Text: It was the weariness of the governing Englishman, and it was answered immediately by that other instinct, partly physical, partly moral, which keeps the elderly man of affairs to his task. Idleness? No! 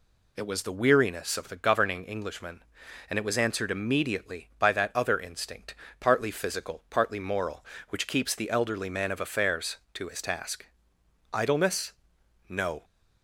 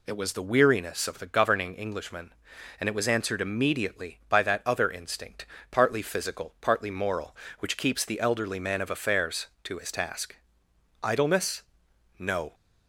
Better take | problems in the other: neither | none

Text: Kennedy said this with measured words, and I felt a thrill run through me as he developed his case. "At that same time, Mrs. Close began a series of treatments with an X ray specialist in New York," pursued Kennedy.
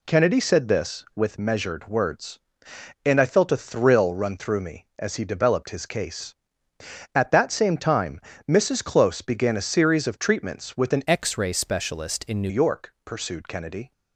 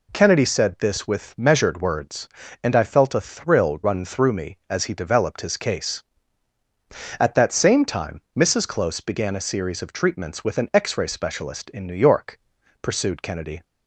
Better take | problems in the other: second | changes voice from "X" to "New"; from 11.0 to 12.5 s; 1.5 s long

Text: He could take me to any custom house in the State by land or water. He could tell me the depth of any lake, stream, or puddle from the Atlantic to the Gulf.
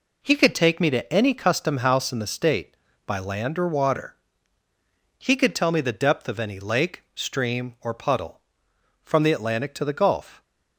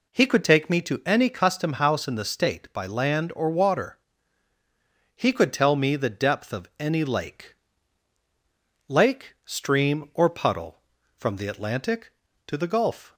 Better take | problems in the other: first | says "lake" twice; at 8.9 s

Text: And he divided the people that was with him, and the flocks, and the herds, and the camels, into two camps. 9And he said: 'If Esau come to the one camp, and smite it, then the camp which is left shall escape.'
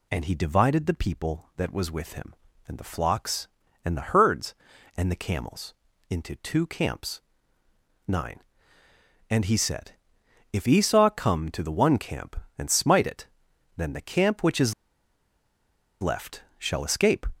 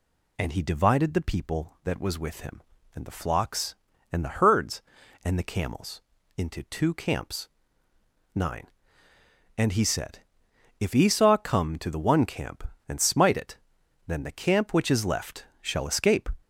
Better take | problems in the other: second | pauses between "is" and "left"; strong; at 14.7 s; 1.2 s long // pauses between "left" and "shall"; slight; at 16.4 s; 0.16 s long; slight in the second

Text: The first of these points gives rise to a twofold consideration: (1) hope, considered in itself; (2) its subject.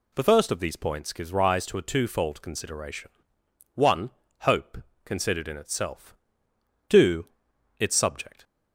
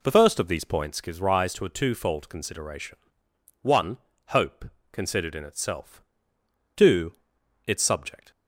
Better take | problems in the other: first | starts louder than the rest; slight; until 1.2 s; 2.5 dB

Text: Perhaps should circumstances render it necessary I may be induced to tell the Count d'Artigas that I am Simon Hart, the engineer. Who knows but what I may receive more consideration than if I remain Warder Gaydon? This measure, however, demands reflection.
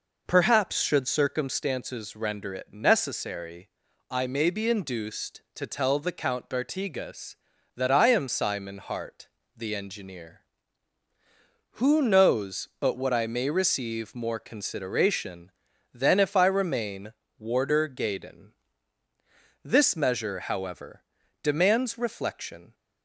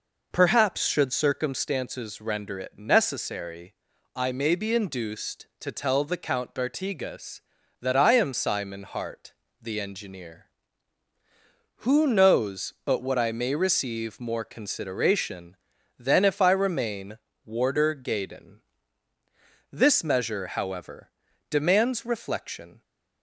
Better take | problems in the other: neither | pauses between "necessary" and "I"; the same in both // pauses between "remain" and "Warder"; slight; the same in both

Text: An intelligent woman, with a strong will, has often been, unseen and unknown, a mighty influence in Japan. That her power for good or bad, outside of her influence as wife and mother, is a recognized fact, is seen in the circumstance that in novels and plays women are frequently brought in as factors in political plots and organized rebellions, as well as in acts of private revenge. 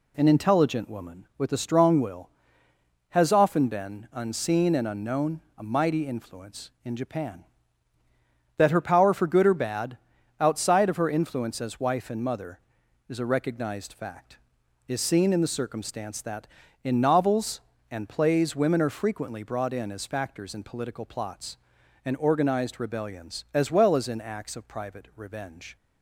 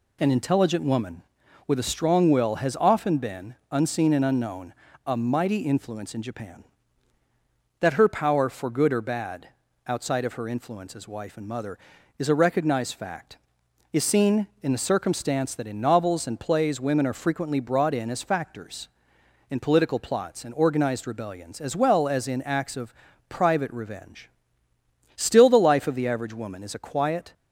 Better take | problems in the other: first | pauses between "of" and "private"; slight; at 22.9 s; 0.34 s long // goes on to say "Still the life of the average woman is a quiet"; strong; from 25.1 s on; 2.1 s long

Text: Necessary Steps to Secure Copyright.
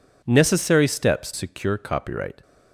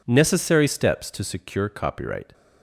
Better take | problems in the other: second | skips "to"; at 1.3 s

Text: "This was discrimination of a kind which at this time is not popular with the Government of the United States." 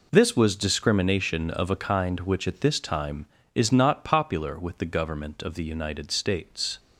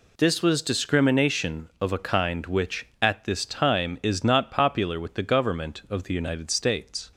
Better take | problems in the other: neither | none

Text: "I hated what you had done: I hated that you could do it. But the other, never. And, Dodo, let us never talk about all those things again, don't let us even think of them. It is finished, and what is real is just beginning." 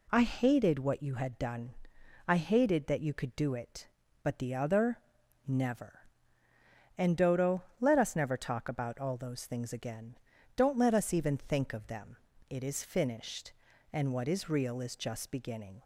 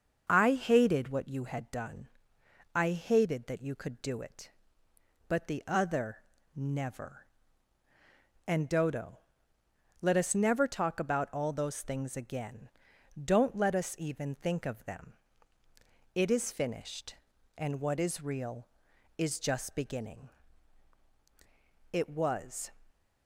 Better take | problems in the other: first | starts louder than the rest; until 1.2 s; 6.5 dB // goes on to say "It was"; noticeable; from 21.9 s on; 0.78 s long

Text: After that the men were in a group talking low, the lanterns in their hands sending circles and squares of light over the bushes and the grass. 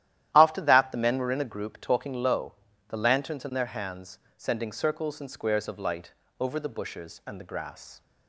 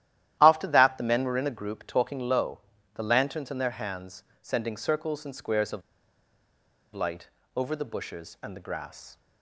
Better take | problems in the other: first | starts louder than the rest; strong; until 1.4 s; 12.5 dB; strong in the first // pauses between "hands" and "sending"; slight; at 4.2 s; 0.18 s long; slight in the first // pauses between "of" and "light"; at 5.8 s; 1.1 s long // pauses between "light" and "over"; slight; at 7.2 s; 0.26 s long; slight in the first

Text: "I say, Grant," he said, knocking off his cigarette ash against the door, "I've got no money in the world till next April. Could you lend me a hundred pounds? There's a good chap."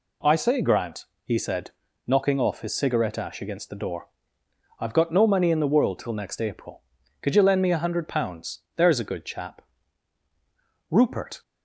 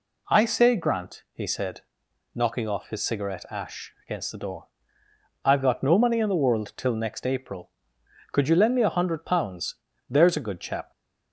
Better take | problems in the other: second | goes on to say "Rupert"; from 10.9 s on; 0.50 s long

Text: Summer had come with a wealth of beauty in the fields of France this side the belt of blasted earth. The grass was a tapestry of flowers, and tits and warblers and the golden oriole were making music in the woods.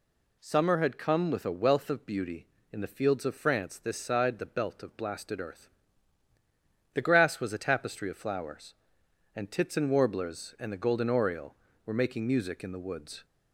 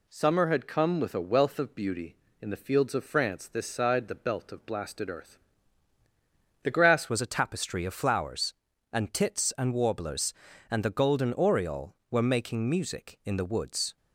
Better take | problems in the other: first | changes voice at "was"; from 7.0 s on; 6.9 s long

